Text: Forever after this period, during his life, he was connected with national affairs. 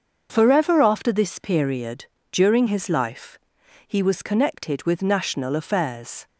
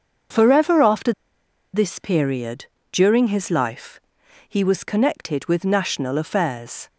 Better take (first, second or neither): first